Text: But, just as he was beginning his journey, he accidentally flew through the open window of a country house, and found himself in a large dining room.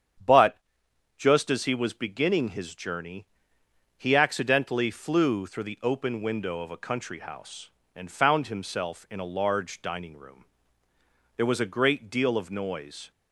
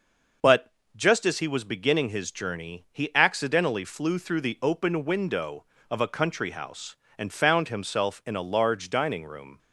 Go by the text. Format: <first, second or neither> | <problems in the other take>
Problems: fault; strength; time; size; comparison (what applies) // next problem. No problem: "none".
second | starts louder than the rest; strong; until 1.8 s; 8.5 dB // goes on to say "There was a great deal of noise"; strong; from 11.3 s on; 1.7 s long